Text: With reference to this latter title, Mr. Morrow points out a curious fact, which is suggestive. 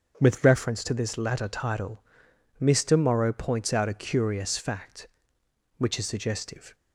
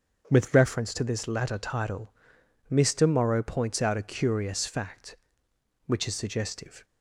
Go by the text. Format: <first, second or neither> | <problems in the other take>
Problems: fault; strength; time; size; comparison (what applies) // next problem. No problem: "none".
neither | starts louder than the rest; the same in both